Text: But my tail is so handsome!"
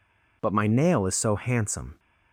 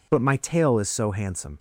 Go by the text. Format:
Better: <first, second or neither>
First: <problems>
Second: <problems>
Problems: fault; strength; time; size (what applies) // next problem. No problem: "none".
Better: second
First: says "nail" for "tail"; at 0.6 s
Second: none